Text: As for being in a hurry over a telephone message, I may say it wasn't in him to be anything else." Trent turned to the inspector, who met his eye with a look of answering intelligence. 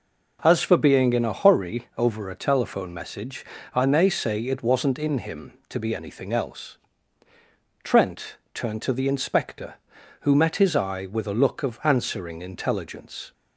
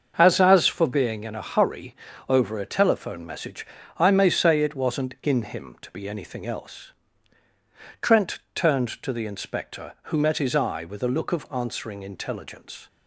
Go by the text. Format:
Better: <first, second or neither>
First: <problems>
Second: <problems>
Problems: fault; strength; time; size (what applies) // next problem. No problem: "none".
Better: first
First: pauses between "Trent" and "turned"; slight; at 8.3 s; 0.16 s long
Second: starts louder than the rest; until 1.1 s; 6.5 dB // says "As" twice; at 0.3 s // pauses between "hurry" and "over"; slight; at 1.9 s; 0.36 s long // pauses between "Trent" and "turned"; slight; at 8.3 s; 0.16 s long